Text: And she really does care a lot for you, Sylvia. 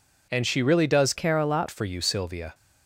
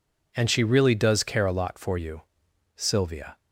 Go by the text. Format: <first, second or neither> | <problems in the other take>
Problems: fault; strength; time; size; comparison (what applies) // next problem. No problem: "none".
second | changes voice from "care" to "lot"; from 1.1 to 1.6 s; 0.5 s long